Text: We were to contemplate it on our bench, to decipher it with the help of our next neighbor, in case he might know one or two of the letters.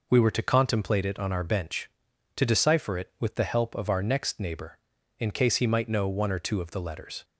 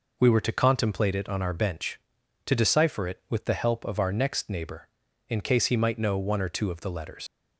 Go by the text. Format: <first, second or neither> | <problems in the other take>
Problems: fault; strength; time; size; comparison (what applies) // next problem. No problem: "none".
first | leaves "letters" unfinished; at 7.2 s; 70 ms